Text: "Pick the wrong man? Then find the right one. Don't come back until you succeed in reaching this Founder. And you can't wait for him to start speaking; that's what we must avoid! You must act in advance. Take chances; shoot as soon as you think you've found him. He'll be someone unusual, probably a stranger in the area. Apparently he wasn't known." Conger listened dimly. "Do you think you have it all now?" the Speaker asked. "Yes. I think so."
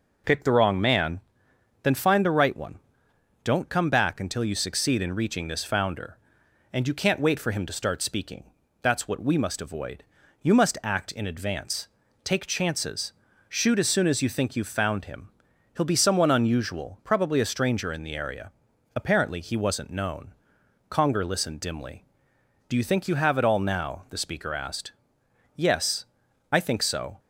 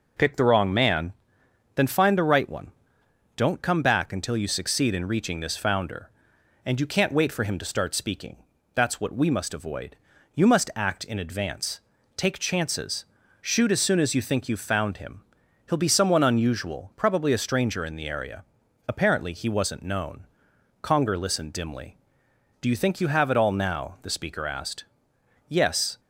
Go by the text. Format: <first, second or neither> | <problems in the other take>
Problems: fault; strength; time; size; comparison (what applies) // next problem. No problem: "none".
first | stops before "I think so"; at 25.9 s